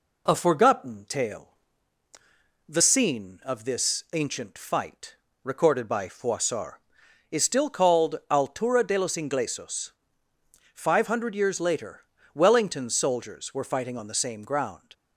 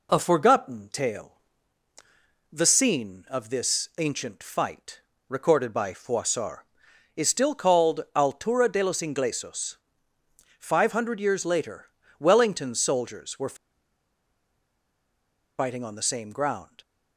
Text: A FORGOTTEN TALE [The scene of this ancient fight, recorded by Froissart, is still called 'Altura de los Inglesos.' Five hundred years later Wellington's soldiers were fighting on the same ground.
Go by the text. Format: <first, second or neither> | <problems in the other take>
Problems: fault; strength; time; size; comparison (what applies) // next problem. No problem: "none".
first | pauses between "TALE" and "The"; at 1.3 s; 1.1 s long; also in the first // pauses between "later" and "Wellington's"; slight; at 11.9 s; 0.28 s long; slight in the first // pauses between "were" and "fighting"; strong; at 13.5 s; 2.0 s long